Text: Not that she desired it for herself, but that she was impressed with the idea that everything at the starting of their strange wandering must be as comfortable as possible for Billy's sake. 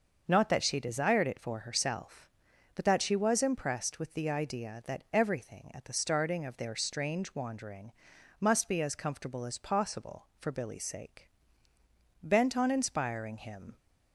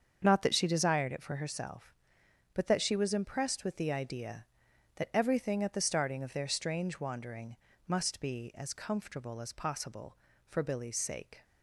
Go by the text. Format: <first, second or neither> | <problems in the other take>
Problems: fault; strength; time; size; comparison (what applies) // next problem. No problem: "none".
second | starts louder than the rest; noticeable; until 1.2 s; 6 dB; also in the second // pauses between "wandering" and "must"; noticeable; at 7.9 s; 0.48 s long; slight in the second // goes on to say "Bent on inspiring him"; from 12.2 s on; 1.5 s long